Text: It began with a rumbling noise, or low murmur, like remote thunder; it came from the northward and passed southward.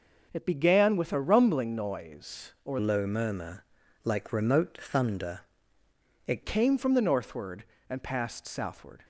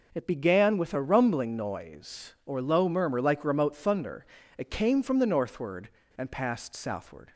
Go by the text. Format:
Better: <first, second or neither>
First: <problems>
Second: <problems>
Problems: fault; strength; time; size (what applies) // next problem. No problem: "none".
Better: second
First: changes voice from "low" to "it"; from 2.7 to 6.4 s; 3.7 s long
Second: none